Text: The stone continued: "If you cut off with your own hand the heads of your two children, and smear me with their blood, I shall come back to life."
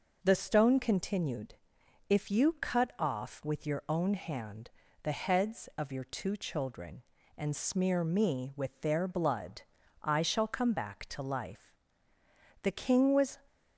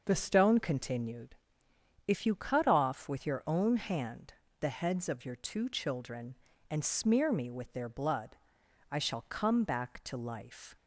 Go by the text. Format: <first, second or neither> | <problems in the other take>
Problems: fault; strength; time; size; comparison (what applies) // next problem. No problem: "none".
second | pauses between "hand" and "the"; slight; at 4.6 s; 0.32 s long; slight in the second // goes on to say "The King was"; noticeable; from 12.6 s on; 0.78 s long